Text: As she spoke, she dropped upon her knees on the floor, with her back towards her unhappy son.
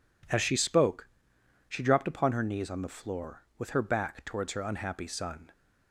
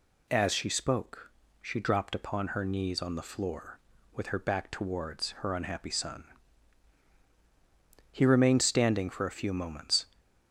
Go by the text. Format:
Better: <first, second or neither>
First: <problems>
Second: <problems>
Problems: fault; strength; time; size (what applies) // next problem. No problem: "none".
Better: first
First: none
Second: goes on to say "He remained standing for a few moments"; strong; from 8.1 s on; 1.9 s long